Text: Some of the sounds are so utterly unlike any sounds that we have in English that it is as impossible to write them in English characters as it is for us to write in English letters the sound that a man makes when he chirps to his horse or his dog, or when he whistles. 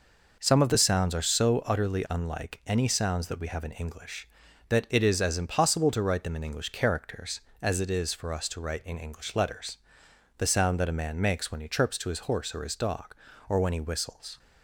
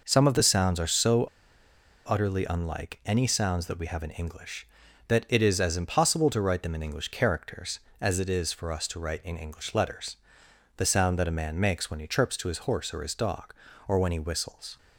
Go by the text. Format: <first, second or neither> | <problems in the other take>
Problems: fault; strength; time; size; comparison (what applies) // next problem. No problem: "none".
first | pauses between "so" and "utterly"; noticeable; at 1.2 s; 0.82 s long // pauses between "letters" and "the"; noticeable; at 10.1 s; 0.62 s long; noticeable in the first